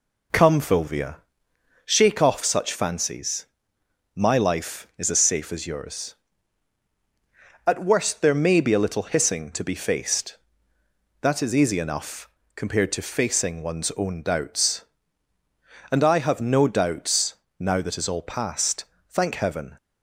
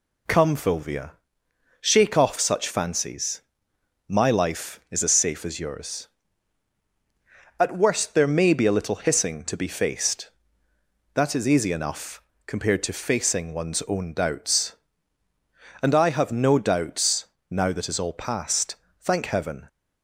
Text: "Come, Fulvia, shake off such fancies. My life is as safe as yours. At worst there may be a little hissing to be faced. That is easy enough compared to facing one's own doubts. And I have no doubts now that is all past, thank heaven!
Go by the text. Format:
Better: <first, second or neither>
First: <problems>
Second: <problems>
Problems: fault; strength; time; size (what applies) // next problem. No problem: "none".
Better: second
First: starts louder than the rest; until 2.0 s; 4 dB // pauses between "enough" and "compared"; slight; at 12.2 s; 0.26 s long // pauses between "doubts" and "now"; slight; at 17.3 s; 0.24 s long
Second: pauses between "enough" and "compared"; slight; at 12.2 s; 0.24 s long // pauses between "doubts" and "now"; slight; at 17.2 s; 0.24 s long